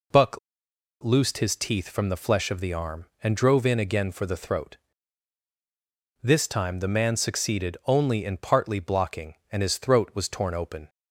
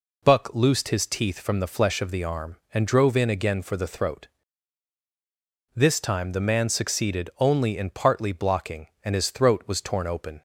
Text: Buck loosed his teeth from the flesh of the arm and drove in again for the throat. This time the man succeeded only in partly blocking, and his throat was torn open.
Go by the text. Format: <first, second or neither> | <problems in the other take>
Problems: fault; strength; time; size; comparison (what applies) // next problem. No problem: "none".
second | pauses between "Buck" and "loosed"; noticeable; at 0.3 s; 0.63 s long